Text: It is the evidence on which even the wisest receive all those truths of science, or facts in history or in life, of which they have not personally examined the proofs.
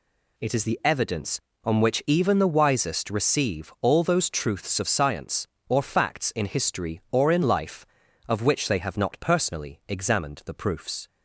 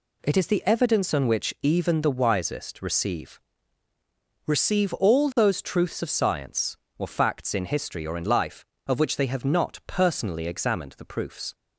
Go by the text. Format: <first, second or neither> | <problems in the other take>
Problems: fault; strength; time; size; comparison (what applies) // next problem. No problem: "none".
first | says "receive" twice; at 4.4 s